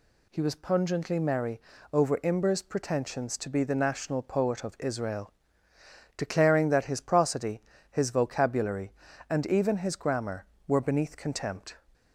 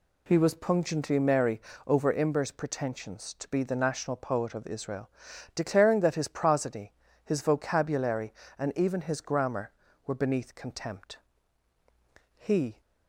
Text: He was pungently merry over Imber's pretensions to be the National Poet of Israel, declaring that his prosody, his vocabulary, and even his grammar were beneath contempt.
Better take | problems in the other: first | pauses between "merry" and "over"; slight; at 1.6 s; 0.26 s long; slight in the first // goes on to say "He"; slight; from 12.3 s on; 0.46 s long

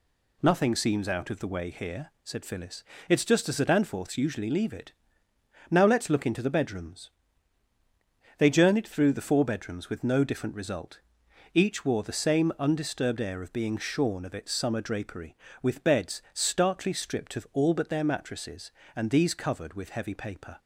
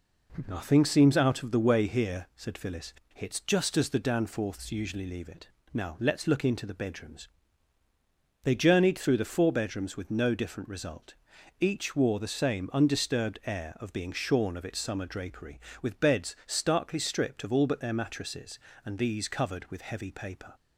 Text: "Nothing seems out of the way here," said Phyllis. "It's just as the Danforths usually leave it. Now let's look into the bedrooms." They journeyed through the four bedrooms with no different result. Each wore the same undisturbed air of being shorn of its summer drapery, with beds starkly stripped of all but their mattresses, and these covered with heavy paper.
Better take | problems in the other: neither | none

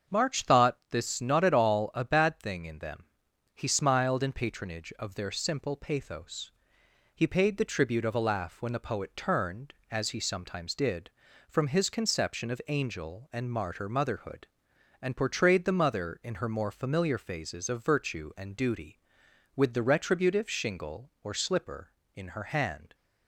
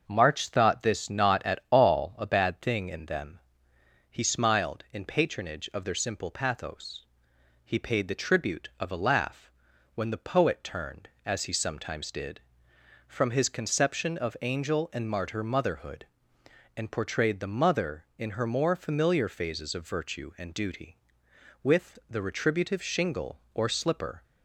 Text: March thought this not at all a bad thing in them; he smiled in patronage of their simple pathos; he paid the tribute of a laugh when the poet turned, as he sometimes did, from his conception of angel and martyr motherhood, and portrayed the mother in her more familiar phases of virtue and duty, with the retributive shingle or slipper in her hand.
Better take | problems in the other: first | starts louder than the rest; until 1.0 s; 6.5 dB; also in the first // pauses between "laugh" and "when"; noticeable; at 9.4 s; 0.46 s long // stops before "in her hand"; at 24.2 s

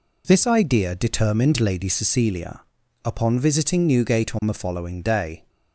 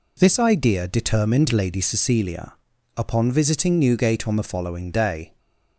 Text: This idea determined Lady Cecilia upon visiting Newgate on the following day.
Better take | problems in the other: neither | pauses between "Cecilia" and "upon"; the same in both

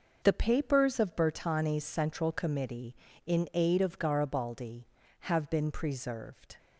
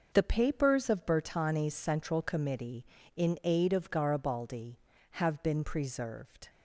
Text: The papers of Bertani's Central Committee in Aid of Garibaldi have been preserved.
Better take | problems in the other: neither | none

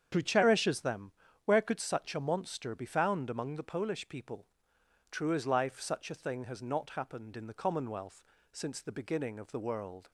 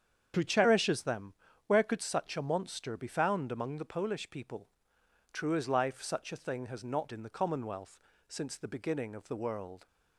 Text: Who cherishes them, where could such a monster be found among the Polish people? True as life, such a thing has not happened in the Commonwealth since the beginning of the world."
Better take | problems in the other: first | starts louder than the rest; strong; until 1.6 s; 8 dB; strong in the first // skips "happened"; at 7.1 s // pauses between "Commonwealth" and "since"; slight; at 7.9 s; 0.30 s long; slight in the first

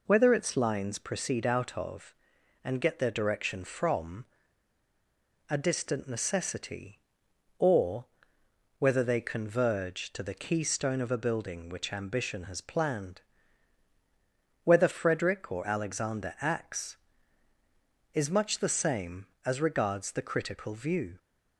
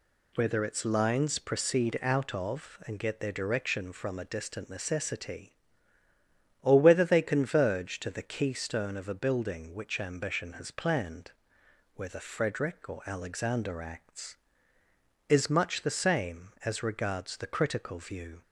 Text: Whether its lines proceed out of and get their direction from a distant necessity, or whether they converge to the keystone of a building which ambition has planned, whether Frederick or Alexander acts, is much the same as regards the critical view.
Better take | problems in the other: second | pauses between "from" and "a"; at 4.2 s; 1.2 s long // pauses between "or" and "whether"; noticeable; at 8.0 s; 0.74 s long

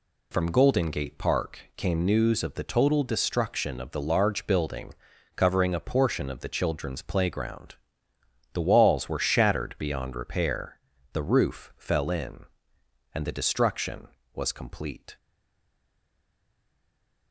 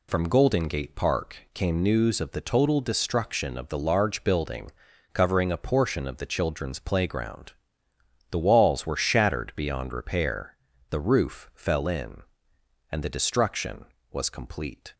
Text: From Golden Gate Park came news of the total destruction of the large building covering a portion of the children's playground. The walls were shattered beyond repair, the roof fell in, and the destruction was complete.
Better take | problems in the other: second | pauses between "Park" and "came"; slight; at 1.6 s; 0.16 s long; slight in the second // pauses between "building" and "covering"; at 4.9 s; 0.42 s long; also in the second // stays silent after the last word; from 15.1 s on; 2.2 s long

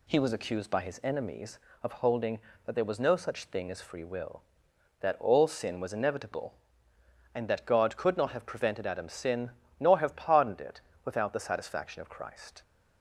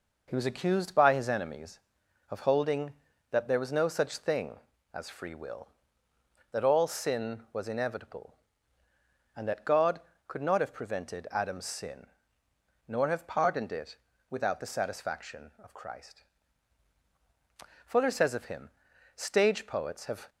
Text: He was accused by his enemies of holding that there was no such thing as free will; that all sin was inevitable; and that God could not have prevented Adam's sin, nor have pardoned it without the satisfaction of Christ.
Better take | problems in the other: first | pauses between "it" and "without"; slight; at 13.9 s; 0.32 s long; slight in the first // goes on to say "Fuller says of him Stage poets have"; strong; from 17.8 s on; 2.4 s long

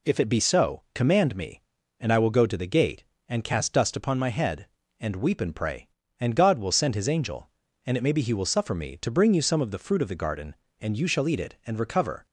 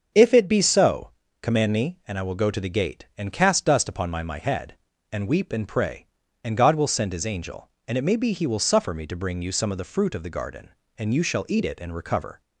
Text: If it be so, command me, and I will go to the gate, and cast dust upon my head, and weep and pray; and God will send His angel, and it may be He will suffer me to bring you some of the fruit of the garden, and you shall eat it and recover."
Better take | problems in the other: first | starts louder than the rest; until 1.4 s; 6.5 dB // says "my" twice; at 4.2 s

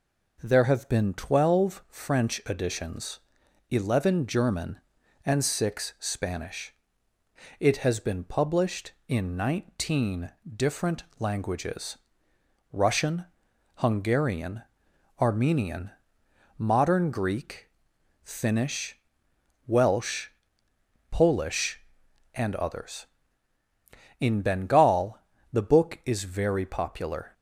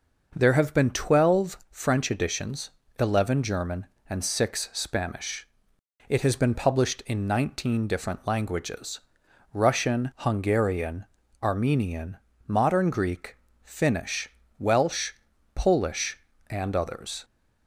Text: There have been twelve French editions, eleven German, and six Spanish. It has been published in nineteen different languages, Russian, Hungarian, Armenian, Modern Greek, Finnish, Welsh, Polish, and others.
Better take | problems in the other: second | pauses between "nineteen" and "different"; slight; at 10.3 s; 0.24 s long // pauses between "different" and "languages"; slight; at 11.0 s; 0.16 s long // goes on to say "In Bengal the book is very popular"; strong; from 24.2 s on; 3.1 s long

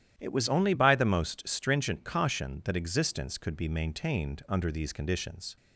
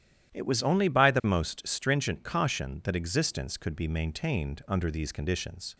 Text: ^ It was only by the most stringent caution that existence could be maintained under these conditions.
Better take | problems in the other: neither | starts louder than the rest; strong; the same in both

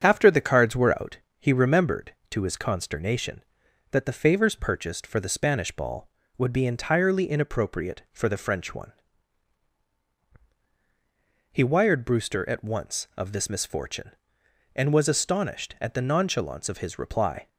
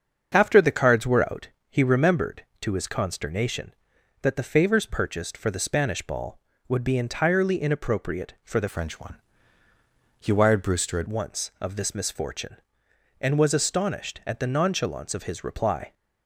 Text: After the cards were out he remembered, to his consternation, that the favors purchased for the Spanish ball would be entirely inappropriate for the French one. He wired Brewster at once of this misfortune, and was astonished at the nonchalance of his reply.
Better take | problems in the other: first | starts louder than the rest; until 1.3 s; 7 dB; strong in the first // pauses between "out" and "he"; slight; at 1.4 s; 0.20 s long; slight in the first // changes voice from "French" to "at"; from 8.6 to 11.0 s; 2.4 s long

